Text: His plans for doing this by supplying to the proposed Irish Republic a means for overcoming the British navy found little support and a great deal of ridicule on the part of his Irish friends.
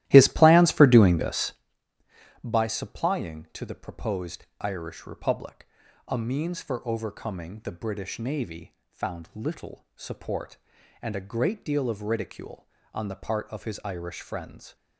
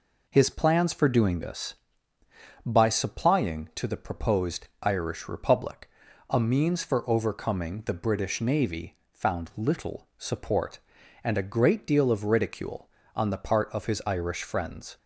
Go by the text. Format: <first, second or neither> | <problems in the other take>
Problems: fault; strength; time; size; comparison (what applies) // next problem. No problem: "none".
second | starts louder than the rest; strong; until 1.7 s; 14.5 dB // pauses between "proposed" and "Irish"; slight; at 4.4 s; 0.16 s long; slight in the second // pauses between "Republic" and "a"; at 5.6 s; 0.40 s long; also in the second // pauses between "navy" and "found"; slight; at 8.7 s; 0.16 s long; slight in the second